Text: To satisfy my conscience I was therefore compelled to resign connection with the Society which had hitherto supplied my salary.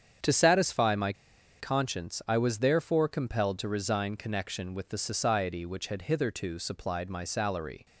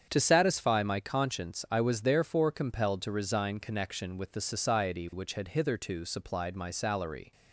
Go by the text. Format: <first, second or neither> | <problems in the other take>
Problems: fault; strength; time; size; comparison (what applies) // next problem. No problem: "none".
second | starts louder than the rest; strong; until 1.7 s; 8 dB; strong in the second // pauses between "my" and "conscience"; noticeable; at 1.1 s; 0.47 s long